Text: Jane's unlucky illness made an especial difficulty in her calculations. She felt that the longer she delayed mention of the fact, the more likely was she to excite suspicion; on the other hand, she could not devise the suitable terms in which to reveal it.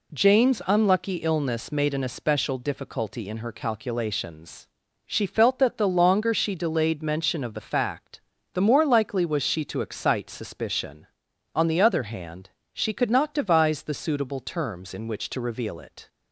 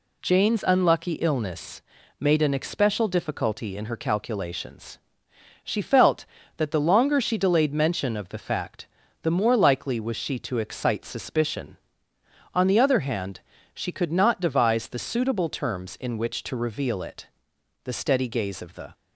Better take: first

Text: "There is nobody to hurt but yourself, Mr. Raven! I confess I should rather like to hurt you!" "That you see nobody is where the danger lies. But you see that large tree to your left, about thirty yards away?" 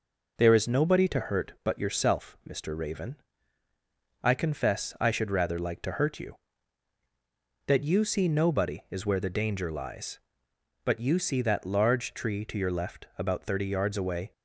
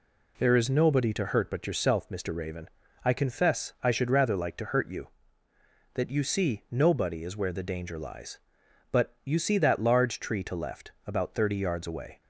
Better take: first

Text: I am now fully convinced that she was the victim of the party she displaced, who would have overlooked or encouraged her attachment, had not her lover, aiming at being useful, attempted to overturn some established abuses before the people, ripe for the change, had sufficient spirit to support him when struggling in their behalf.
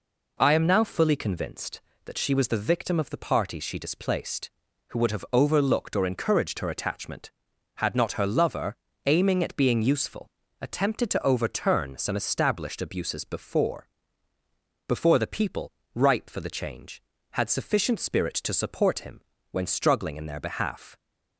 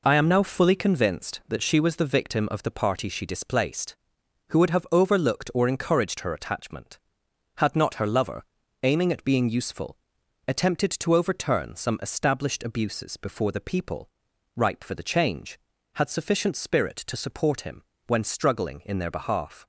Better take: second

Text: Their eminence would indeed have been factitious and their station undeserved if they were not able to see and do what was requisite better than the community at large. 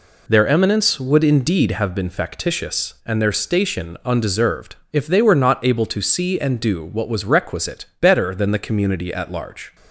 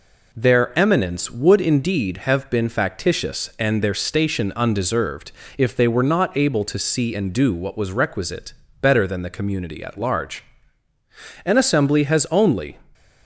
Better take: first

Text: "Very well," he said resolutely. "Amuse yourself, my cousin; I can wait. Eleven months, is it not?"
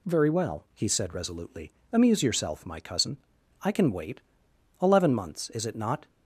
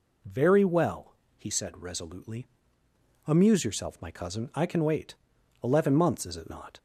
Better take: neither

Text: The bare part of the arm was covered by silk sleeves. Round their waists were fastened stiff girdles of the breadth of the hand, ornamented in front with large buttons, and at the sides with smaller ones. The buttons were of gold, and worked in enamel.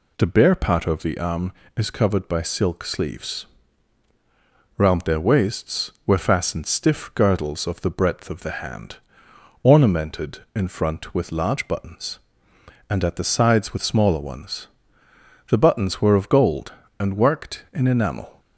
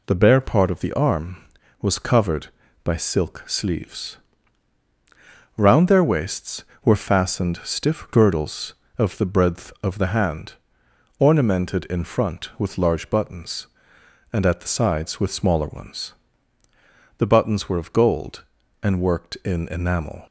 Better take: second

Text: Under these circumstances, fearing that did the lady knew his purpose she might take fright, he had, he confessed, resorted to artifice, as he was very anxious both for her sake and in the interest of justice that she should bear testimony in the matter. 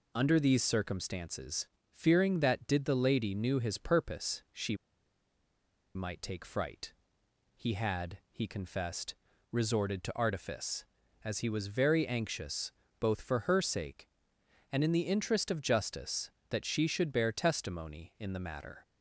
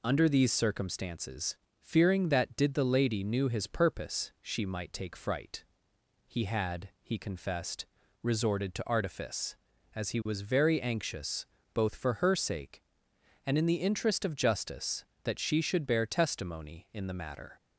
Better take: second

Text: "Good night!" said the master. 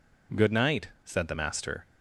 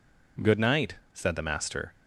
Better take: neither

